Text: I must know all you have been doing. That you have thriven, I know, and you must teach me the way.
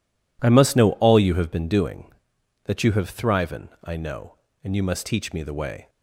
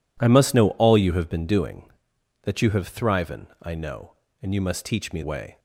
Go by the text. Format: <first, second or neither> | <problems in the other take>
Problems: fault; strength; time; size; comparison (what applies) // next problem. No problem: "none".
first | skips "the"; at 5.2 s